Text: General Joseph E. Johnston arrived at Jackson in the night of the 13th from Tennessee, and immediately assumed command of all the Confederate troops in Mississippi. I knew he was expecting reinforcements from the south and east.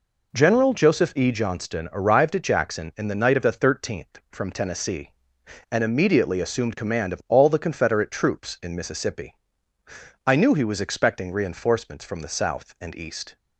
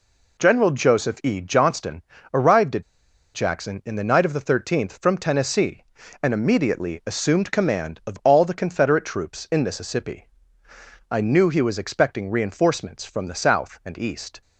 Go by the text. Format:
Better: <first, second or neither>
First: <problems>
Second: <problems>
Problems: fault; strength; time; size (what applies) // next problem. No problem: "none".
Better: first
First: none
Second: pauses between "Johnston" and "arrived"; slight; at 2.0 s; 0.30 s long // pauses between "at" and "Jackson"; noticeable; at 2.8 s; 0.51 s long